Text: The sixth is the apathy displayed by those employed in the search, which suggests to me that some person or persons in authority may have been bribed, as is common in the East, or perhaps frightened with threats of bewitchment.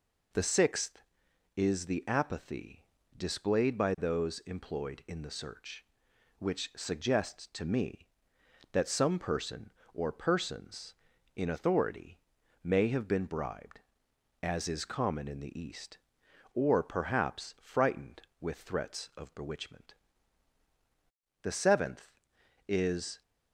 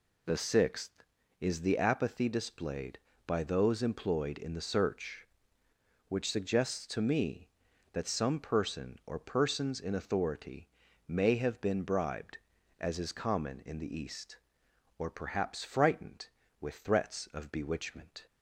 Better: second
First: pauses between "apathy" and "displayed"; slight; at 2.8 s; 0.32 s long // pauses between "authority" and "may"; noticeable; at 12.1 s; 0.46 s long // goes on to say "The seventh is"; strong; from 21.4 s on; 1.8 s long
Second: pauses between "authority" and "may"; at 10.6 s; 0.40 s long

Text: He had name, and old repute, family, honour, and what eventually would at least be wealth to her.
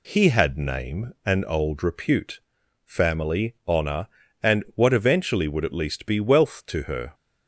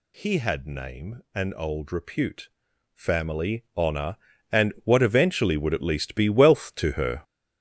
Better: first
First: none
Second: gets louder; strong; throughout; 10.5 dB

